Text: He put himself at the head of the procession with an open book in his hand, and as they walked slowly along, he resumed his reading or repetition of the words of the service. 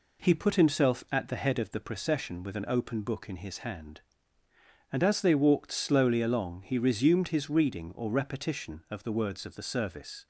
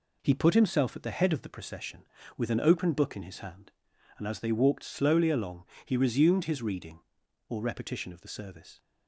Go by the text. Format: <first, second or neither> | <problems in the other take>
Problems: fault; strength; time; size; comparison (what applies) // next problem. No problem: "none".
first | skips "words of the"; at 8.2 s